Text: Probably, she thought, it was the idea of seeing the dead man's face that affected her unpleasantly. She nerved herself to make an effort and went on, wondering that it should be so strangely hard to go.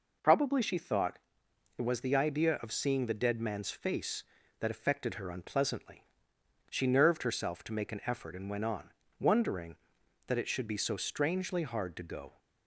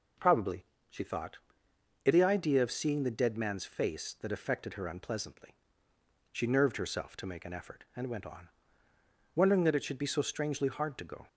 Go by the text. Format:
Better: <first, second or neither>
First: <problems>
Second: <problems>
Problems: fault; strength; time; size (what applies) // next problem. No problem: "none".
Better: first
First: none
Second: skips "was"; at 2.1 s